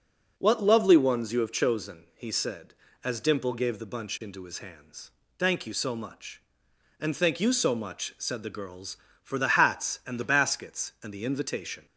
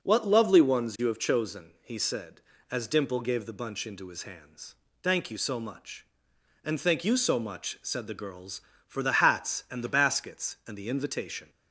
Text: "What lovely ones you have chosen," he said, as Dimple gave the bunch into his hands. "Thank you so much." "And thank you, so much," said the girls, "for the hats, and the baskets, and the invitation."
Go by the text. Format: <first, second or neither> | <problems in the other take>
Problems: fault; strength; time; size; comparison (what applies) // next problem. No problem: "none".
neither | none